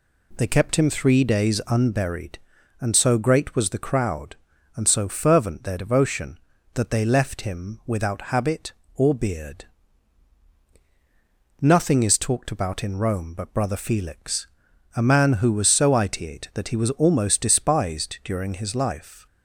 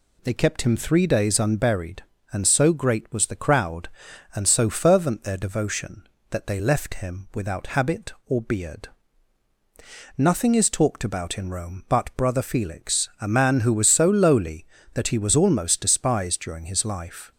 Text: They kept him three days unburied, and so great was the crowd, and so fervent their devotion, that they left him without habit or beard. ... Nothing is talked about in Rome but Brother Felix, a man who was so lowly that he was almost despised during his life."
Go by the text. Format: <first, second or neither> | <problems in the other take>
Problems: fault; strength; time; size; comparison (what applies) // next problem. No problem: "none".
second | says "itiate" for "lowly"; at 15.9 s